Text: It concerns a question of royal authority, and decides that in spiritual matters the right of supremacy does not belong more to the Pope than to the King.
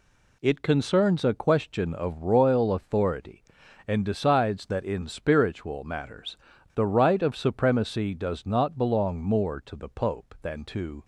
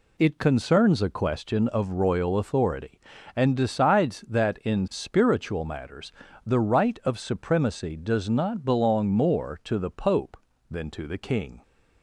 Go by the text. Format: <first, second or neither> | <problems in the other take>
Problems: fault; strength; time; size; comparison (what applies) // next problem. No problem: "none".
second | pauses between "matters" and "the"; at 6.3 s; 0.38 s long; slight in the second // stops before "the King"; at 11.0 s